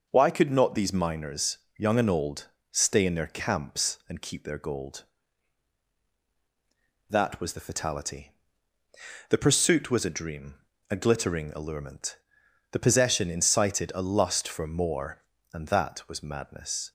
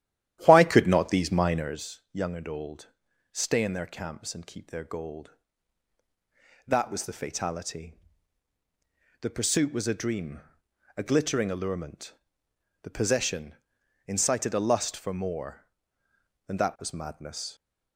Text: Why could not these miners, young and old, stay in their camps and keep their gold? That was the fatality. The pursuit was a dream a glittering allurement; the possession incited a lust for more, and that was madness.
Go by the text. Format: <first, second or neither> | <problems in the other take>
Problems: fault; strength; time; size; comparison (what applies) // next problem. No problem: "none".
first | starts louder than the rest; strong; until 1.8 s; 12 dB // pauses between "dream" and "a"; noticeable; at 10.4 s; 0.56 s long; slight in the first // pauses between "possession" and "incited"; noticeable; at 13.5 s; 0.52 s long